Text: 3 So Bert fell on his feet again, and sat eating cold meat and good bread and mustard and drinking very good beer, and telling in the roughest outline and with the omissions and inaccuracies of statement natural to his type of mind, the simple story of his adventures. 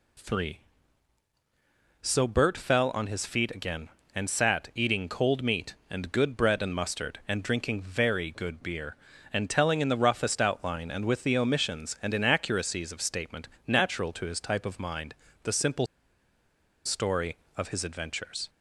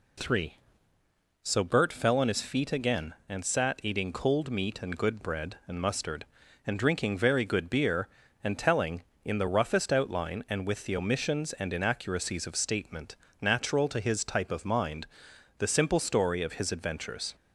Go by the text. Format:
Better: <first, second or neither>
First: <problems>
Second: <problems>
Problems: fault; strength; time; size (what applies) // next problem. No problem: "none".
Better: second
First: pauses between "statement" and "natural"; slight; at 13.4 s; 0.18 s long // pauses between "simple" and "story"; at 15.8 s; 0.99 s long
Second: pauses between "statement" and "natural"; slight; at 13.1 s; 0.24 s long